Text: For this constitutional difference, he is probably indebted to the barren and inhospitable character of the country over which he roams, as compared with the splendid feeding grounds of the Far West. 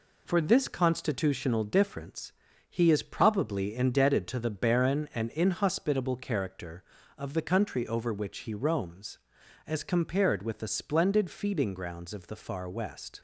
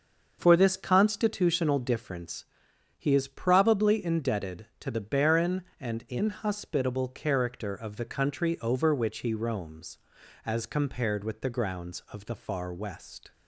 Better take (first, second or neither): first